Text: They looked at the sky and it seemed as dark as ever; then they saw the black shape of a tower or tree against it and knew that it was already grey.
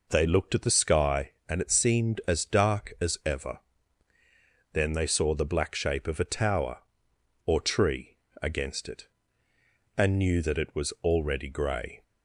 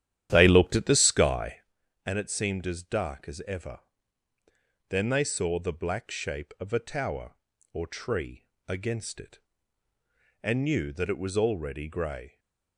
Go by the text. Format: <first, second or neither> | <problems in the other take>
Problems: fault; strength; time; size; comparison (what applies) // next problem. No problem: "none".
first | starts louder than the rest; strong; until 1.7 s; 11 dB // pauses between "tree" and "against"; slight; at 8.4 s; 0.18 s long; slight in the first